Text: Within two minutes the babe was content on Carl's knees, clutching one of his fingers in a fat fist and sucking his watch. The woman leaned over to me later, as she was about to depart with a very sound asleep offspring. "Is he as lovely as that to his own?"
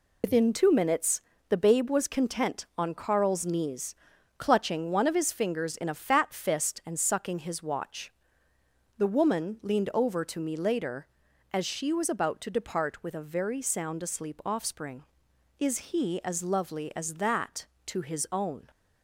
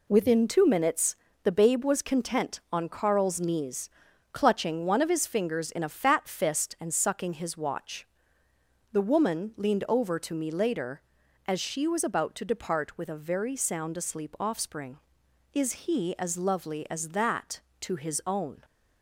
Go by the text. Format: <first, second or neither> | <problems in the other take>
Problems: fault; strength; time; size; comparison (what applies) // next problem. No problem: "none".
second | loses the start of "Within"; at 0.2 s; 100 ms // pauses between "minutes" and "the"; slight; at 1.1 s; 0.28 s long; slight in the second